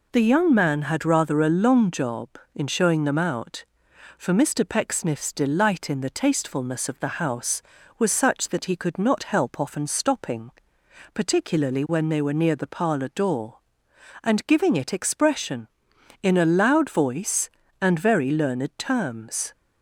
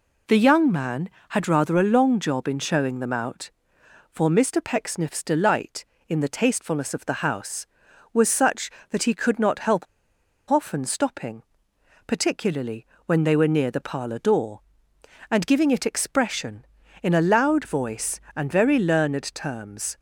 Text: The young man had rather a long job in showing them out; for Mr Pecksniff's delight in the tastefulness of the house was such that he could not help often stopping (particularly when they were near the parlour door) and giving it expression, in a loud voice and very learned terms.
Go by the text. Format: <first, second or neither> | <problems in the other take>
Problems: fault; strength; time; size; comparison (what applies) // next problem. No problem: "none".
first | pauses between "help" and "often"; noticeable; at 9.8 s; 0.65 s long // pauses between "particularly" and "when"; slight; at 12.8 s; 0.18 s long